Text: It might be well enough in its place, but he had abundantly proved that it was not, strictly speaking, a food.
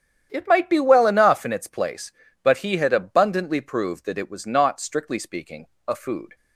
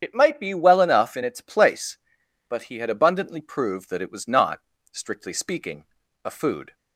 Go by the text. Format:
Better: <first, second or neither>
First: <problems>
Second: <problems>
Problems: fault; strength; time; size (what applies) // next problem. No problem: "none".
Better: first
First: starts louder than the rest; strong; until 1.3 s; 9.5 dB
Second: loses the start of "It"; at 0.0 s; 35 ms // starts louder than the rest; strong; until 1.0 s; 8.5 dB